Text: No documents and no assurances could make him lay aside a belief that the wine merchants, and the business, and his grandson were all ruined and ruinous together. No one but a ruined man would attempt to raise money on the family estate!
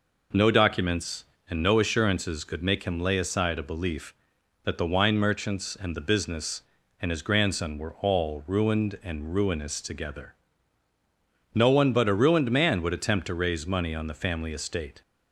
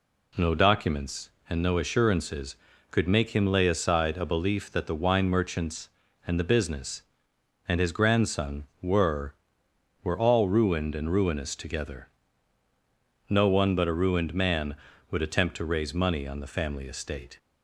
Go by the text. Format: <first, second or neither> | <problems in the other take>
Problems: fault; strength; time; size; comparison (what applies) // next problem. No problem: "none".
first | says "were" twice; at 10.0 s